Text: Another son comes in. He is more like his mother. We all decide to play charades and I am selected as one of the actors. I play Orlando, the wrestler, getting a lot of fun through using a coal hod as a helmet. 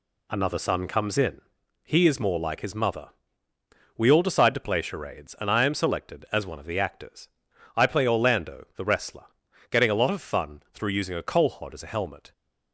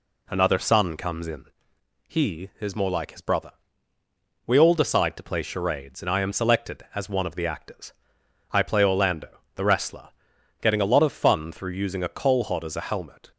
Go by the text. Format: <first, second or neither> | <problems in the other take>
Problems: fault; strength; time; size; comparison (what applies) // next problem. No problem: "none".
first | says "brother" for "mother"; at 3.2 s